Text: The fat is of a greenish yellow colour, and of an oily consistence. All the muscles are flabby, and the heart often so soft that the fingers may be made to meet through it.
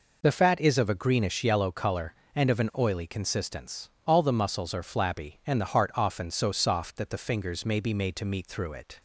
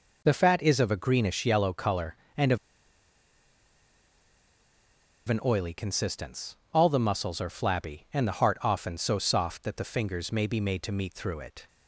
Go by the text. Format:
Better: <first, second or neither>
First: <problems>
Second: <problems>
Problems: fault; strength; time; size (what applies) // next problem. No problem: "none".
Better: first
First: none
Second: pauses between "of" and "an"; strong; at 2.5 s; 2.7 s long